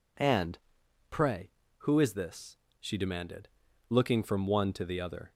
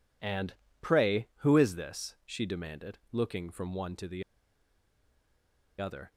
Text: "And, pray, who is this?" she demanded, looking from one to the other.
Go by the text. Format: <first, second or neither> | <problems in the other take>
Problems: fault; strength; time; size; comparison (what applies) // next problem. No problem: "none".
first | pauses between "the" and "other"; strong; at 4.2 s; 1.5 s long